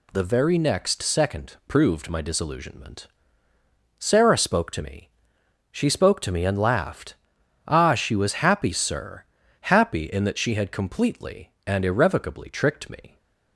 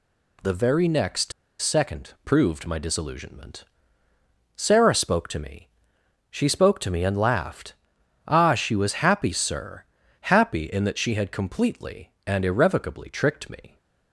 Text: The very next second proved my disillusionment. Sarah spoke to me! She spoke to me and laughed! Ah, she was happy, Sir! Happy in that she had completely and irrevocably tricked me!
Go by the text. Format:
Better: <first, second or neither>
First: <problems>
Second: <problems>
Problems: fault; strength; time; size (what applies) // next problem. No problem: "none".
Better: first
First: none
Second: pauses between "next" and "second"; slight; at 1.3 s; 0.28 s long